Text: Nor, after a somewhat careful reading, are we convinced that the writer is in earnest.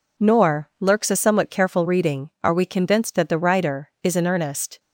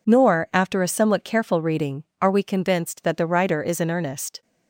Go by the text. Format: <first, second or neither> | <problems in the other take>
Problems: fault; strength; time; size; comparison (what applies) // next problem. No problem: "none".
second | says "lurks" for "after"; at 0.7 s